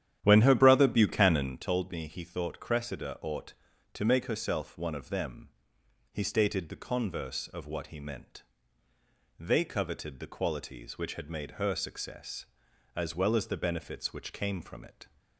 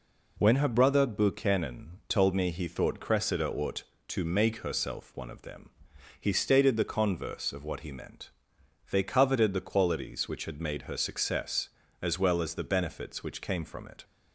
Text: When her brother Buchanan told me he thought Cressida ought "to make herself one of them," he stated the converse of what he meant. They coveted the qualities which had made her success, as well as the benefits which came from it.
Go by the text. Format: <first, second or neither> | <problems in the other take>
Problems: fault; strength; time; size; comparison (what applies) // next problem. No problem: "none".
second | starts louder than the rest; strong; until 1.6 s; 10.5 dB